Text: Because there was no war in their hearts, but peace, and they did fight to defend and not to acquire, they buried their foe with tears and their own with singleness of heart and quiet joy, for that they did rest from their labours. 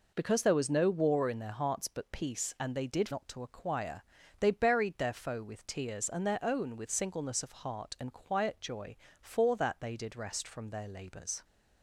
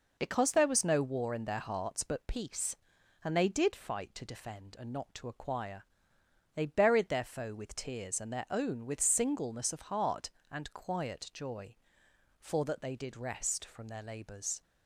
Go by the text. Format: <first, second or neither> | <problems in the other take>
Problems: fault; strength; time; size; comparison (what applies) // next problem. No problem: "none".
second | skips "fight to defend and"; at 3.0 s